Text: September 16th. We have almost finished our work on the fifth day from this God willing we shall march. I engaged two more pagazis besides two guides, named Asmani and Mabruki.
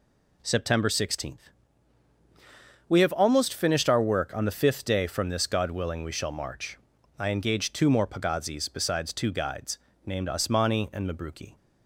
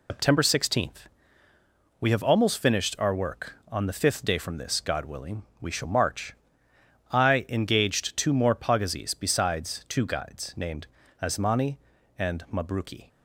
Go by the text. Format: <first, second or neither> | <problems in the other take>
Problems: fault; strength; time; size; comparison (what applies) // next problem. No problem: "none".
first | loses the start of "September"; at 0.0 s; 150 ms // pauses between "willing" and "we"; slight; at 5.4 s; 0.18 s long // pauses between "named" and "Asmani"; slight; at 10.8 s; 0.36 s long